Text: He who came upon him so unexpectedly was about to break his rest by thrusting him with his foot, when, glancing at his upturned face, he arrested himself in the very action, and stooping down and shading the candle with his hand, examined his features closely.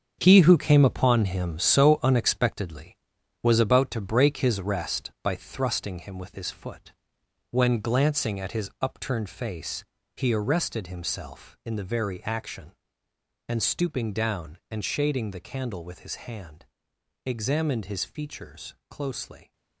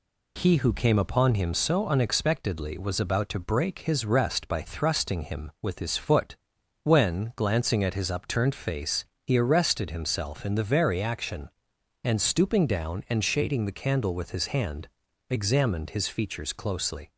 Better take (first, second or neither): second